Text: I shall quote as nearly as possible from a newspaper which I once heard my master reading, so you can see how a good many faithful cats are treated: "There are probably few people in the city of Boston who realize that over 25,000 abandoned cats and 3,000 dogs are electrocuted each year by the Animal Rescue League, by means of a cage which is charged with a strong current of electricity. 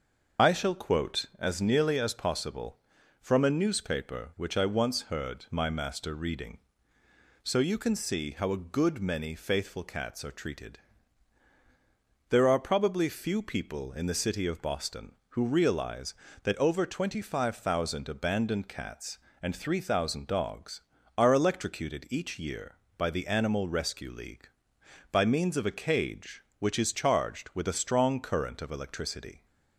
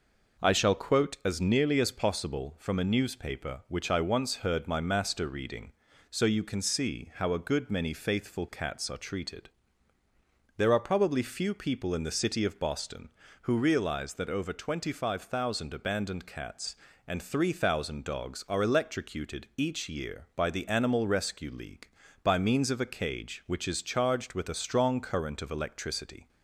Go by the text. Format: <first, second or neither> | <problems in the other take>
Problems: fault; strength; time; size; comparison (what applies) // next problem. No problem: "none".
second | loses the start of "I"; at 0.3 s; 50 ms // starts louder than the rest; until 1.5 s; 6.5 dB